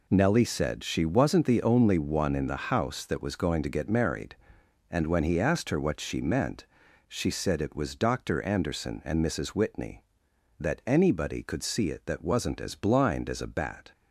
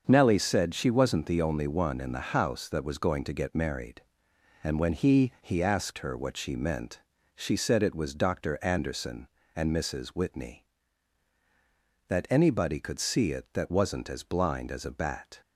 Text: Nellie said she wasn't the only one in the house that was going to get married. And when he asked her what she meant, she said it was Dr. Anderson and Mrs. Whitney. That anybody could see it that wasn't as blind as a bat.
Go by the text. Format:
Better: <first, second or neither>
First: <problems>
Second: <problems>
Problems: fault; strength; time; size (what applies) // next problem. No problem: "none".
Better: first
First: none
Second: starts louder than the rest; until 1.0 s; 6.5 dB // says "he" twice; at 5.4 s